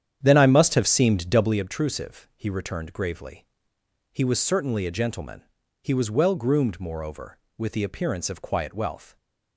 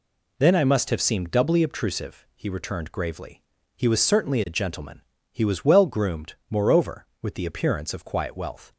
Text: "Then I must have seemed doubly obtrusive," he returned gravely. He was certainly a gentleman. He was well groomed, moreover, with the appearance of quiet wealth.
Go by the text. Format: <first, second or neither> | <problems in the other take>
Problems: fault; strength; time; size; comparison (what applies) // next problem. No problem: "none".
second | starts louder than the rest; strong; until 1.6 s; 9.5 dB